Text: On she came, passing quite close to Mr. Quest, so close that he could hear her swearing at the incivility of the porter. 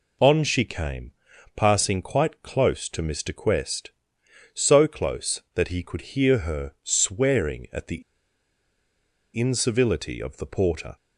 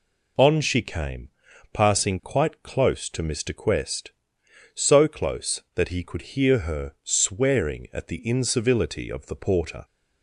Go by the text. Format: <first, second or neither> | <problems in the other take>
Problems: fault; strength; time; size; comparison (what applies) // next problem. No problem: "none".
second | pauses between "the" and "incivility"; strong; at 8.0 s; 1.3 s long